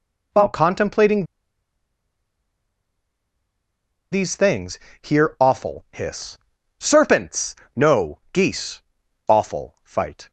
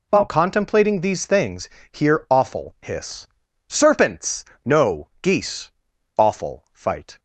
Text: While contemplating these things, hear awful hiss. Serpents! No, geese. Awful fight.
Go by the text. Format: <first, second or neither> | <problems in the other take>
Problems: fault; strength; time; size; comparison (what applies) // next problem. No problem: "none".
second | pauses between "contemplating" and "these"; strong; at 1.2 s; 2.8 s long